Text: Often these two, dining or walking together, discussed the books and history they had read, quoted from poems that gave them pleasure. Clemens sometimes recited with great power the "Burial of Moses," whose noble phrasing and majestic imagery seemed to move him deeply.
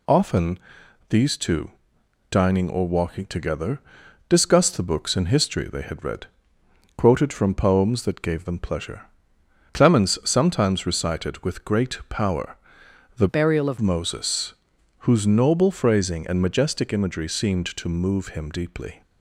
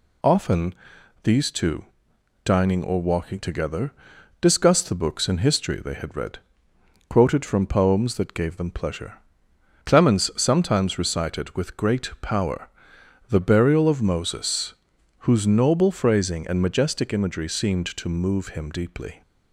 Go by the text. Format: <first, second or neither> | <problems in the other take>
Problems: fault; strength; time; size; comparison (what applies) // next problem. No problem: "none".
second | pauses between "Often" and "these"; noticeable; at 0.5 s; 0.50 s long; noticeable in the second // pauses between "power" and "the"; noticeable; at 12.5 s; 0.62 s long; noticeable in the second // changes voice from "Burial" to "of"; from 13.2 to 13.7 s; 0.5 s long